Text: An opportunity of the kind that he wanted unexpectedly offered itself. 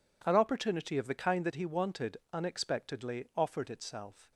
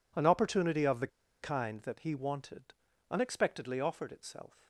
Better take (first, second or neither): first